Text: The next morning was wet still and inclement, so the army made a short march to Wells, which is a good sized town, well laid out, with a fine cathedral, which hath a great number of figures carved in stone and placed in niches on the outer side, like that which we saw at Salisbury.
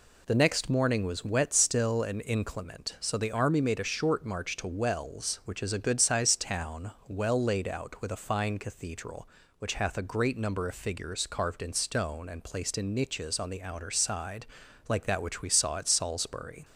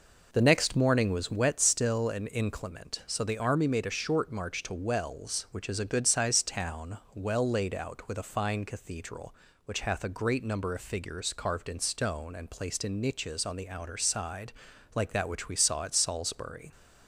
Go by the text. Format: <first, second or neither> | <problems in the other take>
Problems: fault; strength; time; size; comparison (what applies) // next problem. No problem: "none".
first | starts louder than the rest; noticeable; until 1.6 s; 5 dB